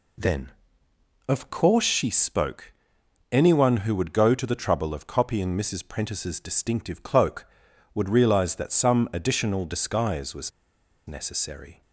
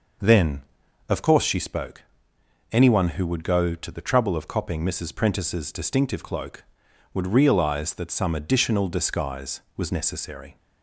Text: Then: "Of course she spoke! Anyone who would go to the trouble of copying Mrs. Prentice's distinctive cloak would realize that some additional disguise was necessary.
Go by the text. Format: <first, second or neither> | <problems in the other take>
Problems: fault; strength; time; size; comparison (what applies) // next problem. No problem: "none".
second | pauses between "was" and "necessary"; noticeable; at 10.5 s; 0.56 s long